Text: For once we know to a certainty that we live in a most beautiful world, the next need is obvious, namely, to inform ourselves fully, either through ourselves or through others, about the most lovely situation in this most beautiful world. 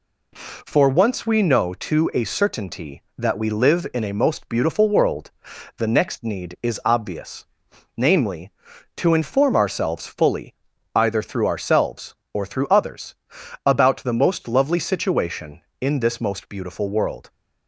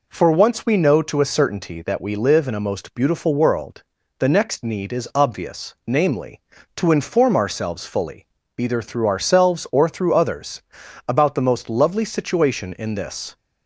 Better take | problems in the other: first | stops before "most beautiful world"; at 13.3 s

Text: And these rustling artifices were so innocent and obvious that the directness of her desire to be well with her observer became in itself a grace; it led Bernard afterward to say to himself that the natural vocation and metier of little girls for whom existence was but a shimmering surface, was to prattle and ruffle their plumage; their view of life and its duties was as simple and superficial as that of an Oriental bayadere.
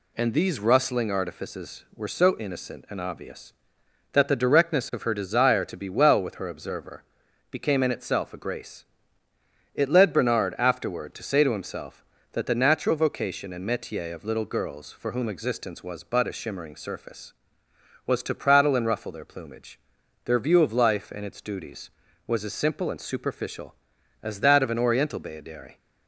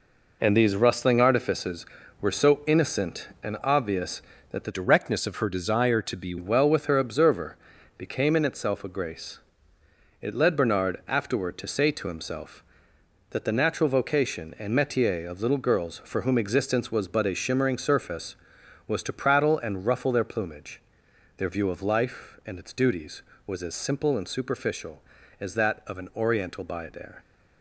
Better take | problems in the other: first | changes voice from "directness" to "be"; from 4.7 to 6.3 s; 1.6 s long // pauses between "observer" and "became"; at 7.5 s; 0.42 s long; noticeable in the first

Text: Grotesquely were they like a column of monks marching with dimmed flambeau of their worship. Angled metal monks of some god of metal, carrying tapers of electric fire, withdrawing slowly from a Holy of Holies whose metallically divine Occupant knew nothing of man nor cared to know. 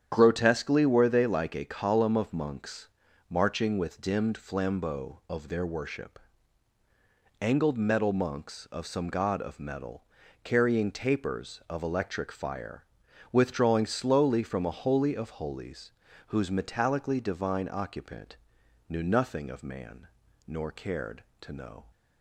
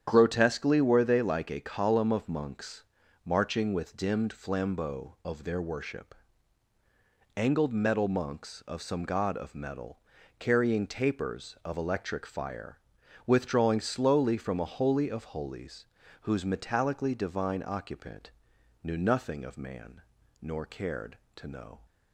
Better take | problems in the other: neither | starts louder than the rest; strong; the same in both // pauses between "monks" and "marching"; the same in both // pauses between "Holies" and "whose"; slight; the same in both // pauses between "Occupant" and "knew"; noticeable; the same in both // pauses between "man" and "nor"; the same in both

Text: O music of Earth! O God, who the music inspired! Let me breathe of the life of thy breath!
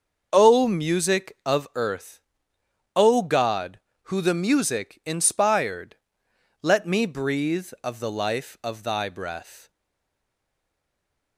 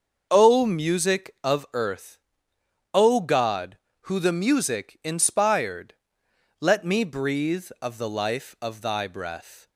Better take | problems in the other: second | starts louder than the rest; until 1.3 s; 6.5 dB; also in the second // stays silent after the last word; noticeable; from 9.6 s on; 1.7 s long

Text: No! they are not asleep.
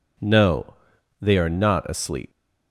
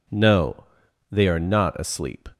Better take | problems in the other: second | leaves "asleep" unfinished; at 2.3 s; 115 ms

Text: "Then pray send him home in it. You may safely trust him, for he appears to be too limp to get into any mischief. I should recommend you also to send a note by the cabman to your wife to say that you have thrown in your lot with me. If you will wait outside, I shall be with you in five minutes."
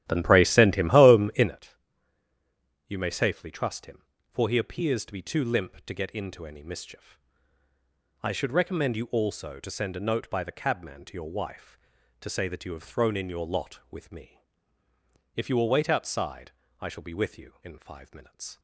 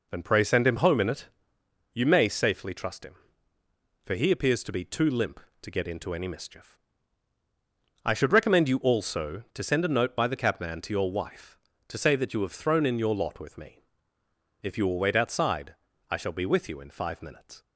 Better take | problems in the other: second | starts louder than the rest; strong; until 1.6 s; 13 dB

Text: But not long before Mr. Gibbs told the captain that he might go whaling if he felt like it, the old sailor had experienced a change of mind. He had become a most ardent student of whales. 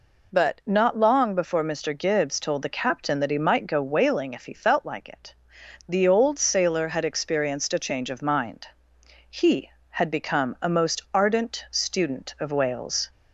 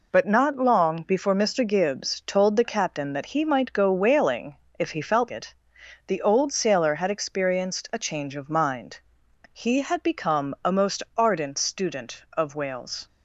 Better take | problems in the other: first | pauses between "whaling" and "if"; slight; at 4.5 s; 0.20 s long // skips "like"; at 5.3 s

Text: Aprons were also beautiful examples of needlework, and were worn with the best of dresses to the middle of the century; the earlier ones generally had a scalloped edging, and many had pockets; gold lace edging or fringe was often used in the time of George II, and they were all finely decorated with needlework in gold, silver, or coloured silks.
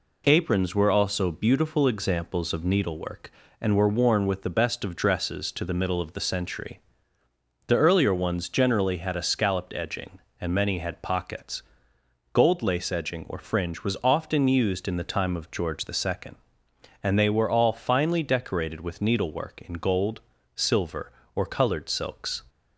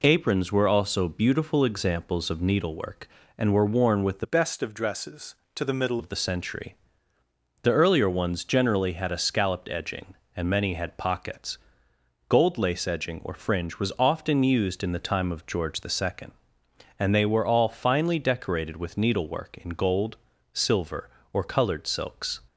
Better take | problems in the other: first | changes voice from "best" to "middle"; from 4.2 to 5.9 s; 1.7 s long

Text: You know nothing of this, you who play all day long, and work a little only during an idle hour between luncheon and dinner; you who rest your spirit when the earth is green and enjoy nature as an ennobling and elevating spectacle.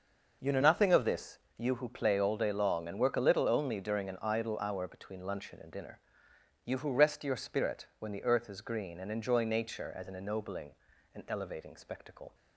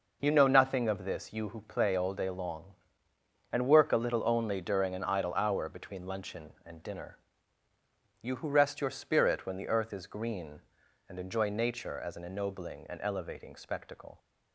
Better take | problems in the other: neither | none

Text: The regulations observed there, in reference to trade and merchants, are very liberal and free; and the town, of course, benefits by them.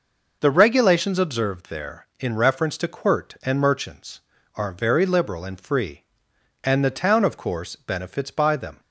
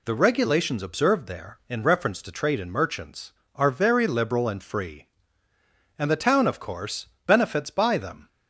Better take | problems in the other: second | says "quirt" for "trade"; at 2.8 s

